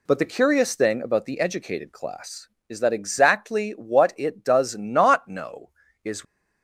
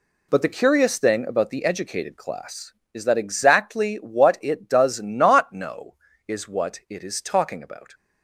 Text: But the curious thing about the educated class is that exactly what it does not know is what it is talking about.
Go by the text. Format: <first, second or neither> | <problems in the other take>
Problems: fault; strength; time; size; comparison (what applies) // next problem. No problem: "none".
second | stops before "what it is talking about"; at 6.2 s